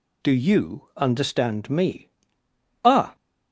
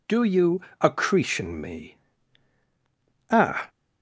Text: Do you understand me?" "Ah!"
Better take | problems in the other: first | says "accretion" for "understand"; at 0.8 s

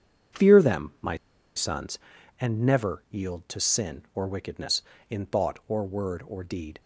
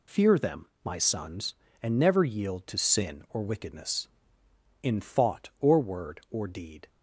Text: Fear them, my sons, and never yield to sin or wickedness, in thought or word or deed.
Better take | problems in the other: second | pauses between "my" and "sons"; at 1.1 s; 0.40 s long

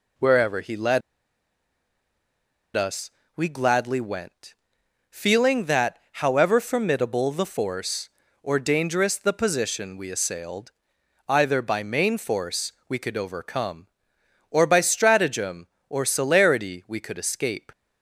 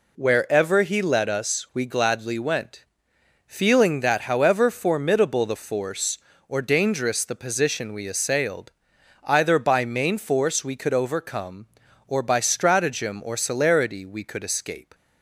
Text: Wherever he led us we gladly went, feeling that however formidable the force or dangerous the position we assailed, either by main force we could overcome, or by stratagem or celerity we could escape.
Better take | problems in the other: second | pauses between "led" and "us"; strong; at 1.0 s; 1.7 s long // pauses between "us" and "we"; slight; at 3.1 s; 0.24 s long // pauses between "that" and "however"; slight; at 5.9 s; 0.16 s long // pauses between "force" and "we"; slight; at 12.7 s; 0.16 s long

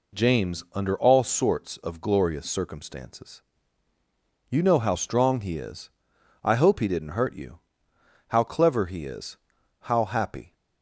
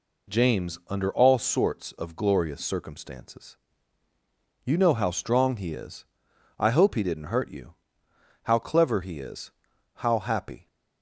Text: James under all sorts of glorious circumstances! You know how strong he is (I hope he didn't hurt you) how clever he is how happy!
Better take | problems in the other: neither | pauses between "is" and "how"; the same in both

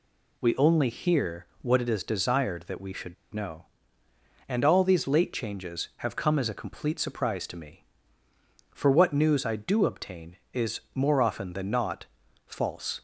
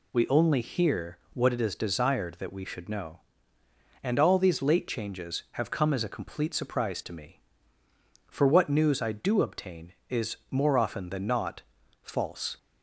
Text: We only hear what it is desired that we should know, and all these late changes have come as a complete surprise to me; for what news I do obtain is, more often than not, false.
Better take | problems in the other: second | pauses between "hear" and "what"; slight; at 1.4 s; 0.16 s long; slight in the second // pauses between "should" and "know"; slight; at 3.1 s; 0.18 s long

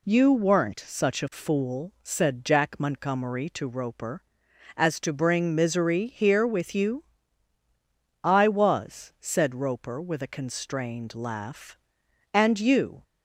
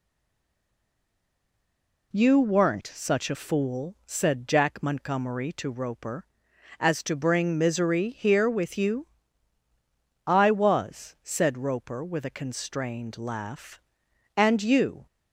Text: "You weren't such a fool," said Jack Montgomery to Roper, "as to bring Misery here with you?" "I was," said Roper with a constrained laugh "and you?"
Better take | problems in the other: first | stays silent before the first word; until 2.1 s; 2.1 s long

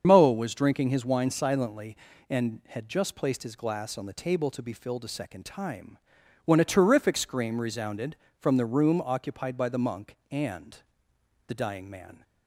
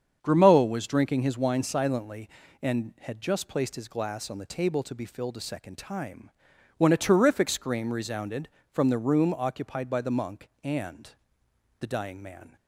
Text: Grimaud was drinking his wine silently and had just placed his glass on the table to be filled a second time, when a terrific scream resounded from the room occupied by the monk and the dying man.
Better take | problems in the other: second | loses the start of "Grimaud"; at 0.0 s; 160 ms // starts louder than the rest; until 1.0 s; 7 dB; strong in the second // pauses between "and" and "the"; noticeable; at 10.7 s; 0.70 s long; noticeable in the second

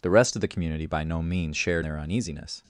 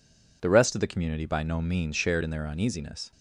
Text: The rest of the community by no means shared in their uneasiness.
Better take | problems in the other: second | skips "in"; at 1.8 s

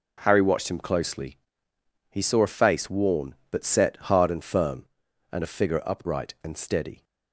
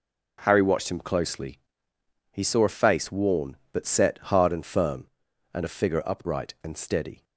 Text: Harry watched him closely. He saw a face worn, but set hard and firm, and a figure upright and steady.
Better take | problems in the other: neither | none

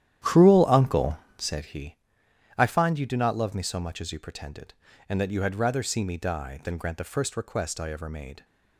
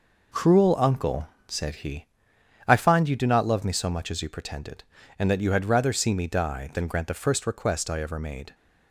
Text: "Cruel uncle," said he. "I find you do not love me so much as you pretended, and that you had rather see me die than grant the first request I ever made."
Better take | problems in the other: second | starts louder than the rest; strong; until 1.7 s; 11 dB

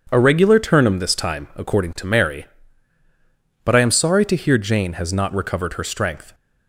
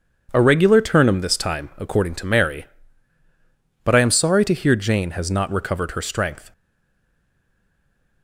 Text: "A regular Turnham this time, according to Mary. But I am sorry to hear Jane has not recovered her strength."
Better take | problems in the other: first | stays silent after the last word; noticeable; from 6.5 s on; 1.7 s long

